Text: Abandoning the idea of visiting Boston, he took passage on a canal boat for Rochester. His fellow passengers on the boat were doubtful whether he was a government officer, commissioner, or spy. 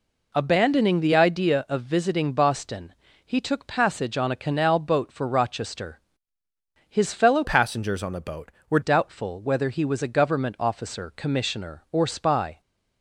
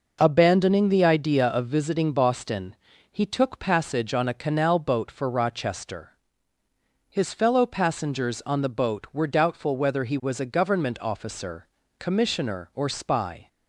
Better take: second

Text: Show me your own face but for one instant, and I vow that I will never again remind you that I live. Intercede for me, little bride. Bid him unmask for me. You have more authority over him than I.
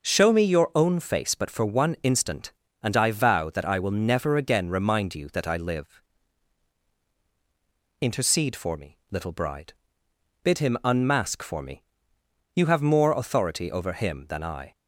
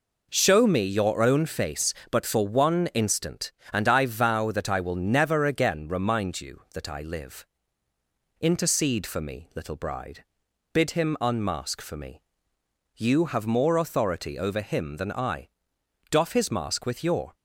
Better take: first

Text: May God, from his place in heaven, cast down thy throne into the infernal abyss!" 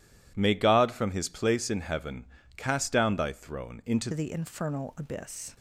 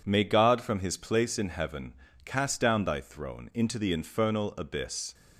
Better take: second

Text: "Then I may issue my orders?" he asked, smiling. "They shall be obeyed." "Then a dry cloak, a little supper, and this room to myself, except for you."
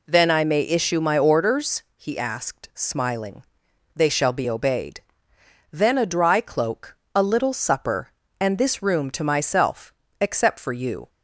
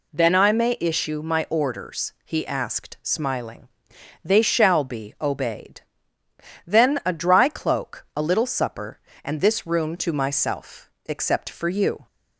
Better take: neither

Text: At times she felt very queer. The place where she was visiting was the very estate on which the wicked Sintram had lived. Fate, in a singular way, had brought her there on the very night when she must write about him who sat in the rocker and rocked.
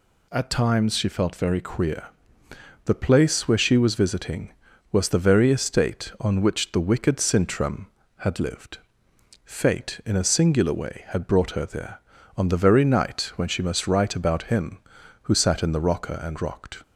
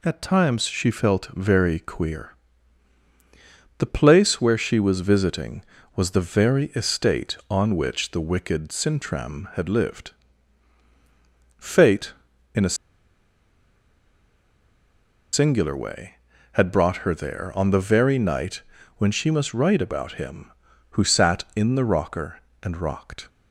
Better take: first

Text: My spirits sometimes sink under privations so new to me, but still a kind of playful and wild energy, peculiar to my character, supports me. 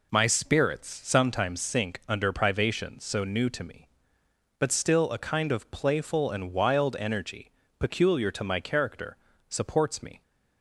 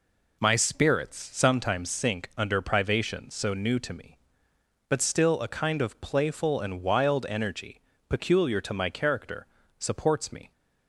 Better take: neither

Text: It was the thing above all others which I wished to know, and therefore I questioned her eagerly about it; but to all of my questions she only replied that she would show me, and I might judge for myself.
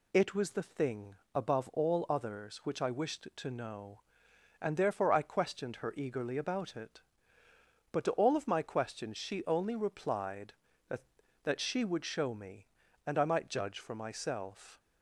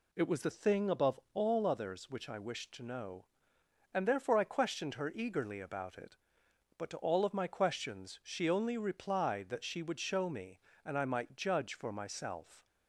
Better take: second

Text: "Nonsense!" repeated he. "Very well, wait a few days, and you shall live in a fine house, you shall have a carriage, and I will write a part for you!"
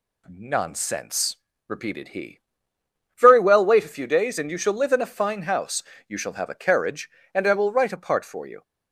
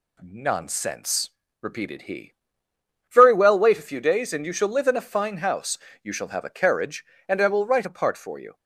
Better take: neither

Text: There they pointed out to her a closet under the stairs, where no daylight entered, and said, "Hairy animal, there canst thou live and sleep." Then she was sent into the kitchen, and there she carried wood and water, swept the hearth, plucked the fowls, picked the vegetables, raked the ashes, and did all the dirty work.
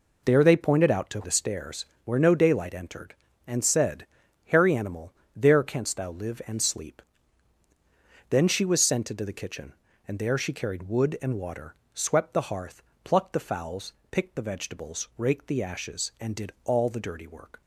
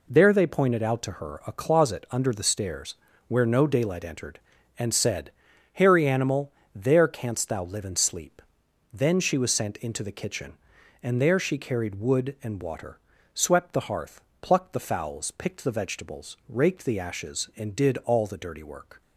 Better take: second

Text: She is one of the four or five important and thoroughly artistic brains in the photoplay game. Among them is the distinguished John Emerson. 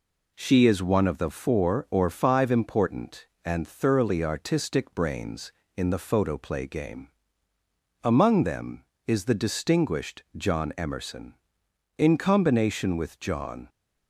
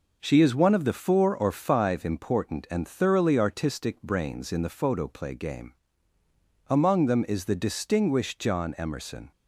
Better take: second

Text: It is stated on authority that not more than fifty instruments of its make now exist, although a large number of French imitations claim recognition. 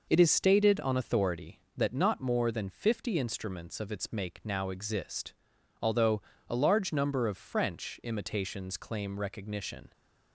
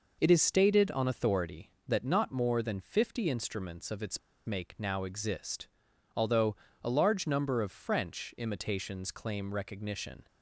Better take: first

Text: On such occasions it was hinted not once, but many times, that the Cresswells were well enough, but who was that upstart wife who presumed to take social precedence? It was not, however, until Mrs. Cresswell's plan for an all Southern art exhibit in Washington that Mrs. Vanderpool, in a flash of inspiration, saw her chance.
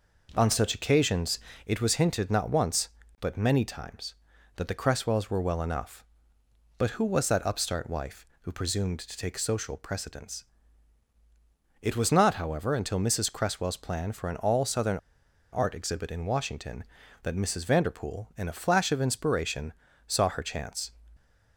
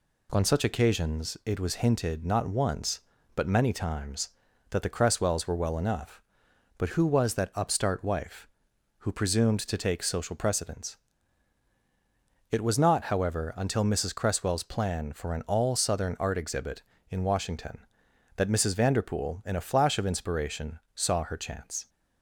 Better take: second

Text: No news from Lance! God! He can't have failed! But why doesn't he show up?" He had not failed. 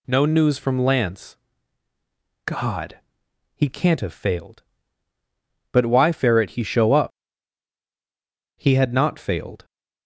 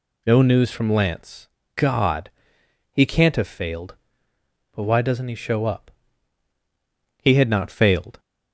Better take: second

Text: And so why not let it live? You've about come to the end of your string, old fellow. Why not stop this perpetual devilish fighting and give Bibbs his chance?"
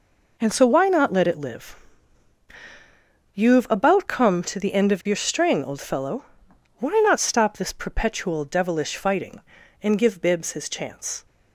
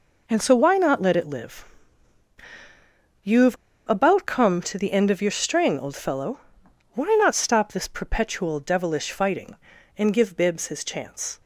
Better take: first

